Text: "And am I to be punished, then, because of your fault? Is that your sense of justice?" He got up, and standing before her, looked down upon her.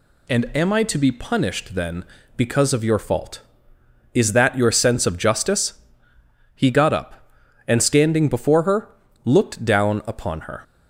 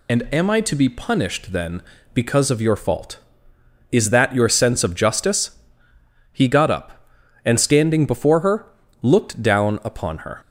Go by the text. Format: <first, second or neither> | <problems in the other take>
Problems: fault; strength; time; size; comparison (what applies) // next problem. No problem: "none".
first | loses the start of "And"; at 0.0 s; 30 ms